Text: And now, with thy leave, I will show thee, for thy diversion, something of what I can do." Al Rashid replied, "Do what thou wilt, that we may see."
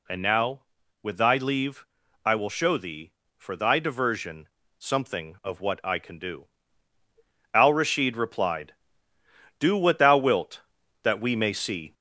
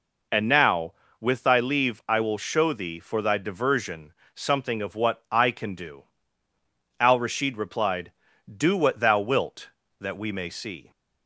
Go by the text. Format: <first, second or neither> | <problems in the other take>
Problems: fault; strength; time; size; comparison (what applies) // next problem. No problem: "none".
second | gets louder; slight; throughout; 3.5 dB